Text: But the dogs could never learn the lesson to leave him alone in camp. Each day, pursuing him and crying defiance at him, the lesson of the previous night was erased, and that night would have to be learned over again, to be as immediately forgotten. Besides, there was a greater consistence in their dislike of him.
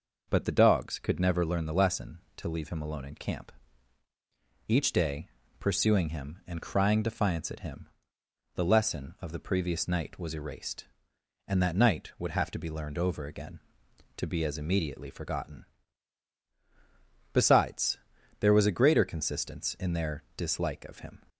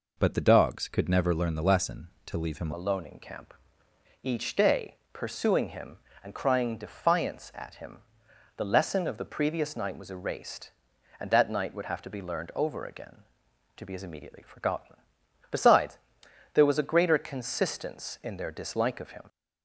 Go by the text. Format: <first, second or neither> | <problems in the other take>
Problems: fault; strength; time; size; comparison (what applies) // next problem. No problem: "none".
first | changes voice at "alone"; from 2.7 s on; 16.5 s long